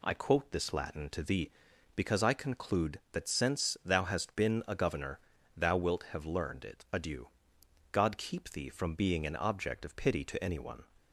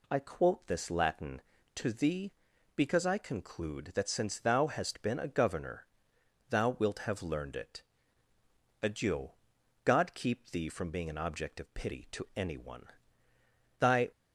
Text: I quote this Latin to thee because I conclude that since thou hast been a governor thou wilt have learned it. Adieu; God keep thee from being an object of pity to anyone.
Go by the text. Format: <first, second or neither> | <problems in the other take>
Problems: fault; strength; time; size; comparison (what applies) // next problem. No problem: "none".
first | pauses between "governor" and "thou"; noticeable; at 5.8 s; 0.64 s long; slight in the first // goes on to say "Thy"; slight; from 13.7 s on; 0.32 s long